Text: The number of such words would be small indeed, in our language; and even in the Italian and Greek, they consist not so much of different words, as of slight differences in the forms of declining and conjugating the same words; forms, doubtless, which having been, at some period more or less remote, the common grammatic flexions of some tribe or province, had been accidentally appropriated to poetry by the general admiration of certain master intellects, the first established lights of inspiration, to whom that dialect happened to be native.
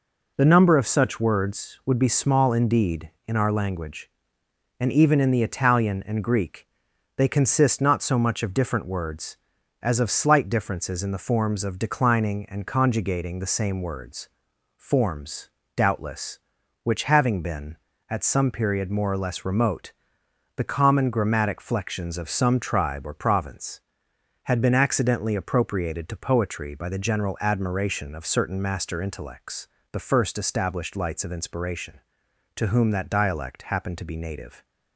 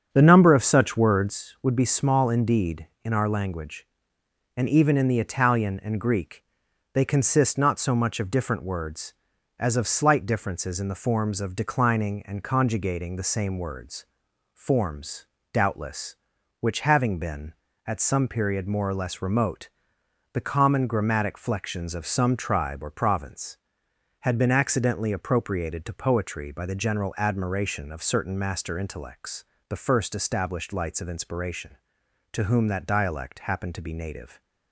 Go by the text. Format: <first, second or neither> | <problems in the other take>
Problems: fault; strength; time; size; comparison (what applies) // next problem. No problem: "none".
first | starts louder than the rest; strong; until 1.5 s; 7.5 dB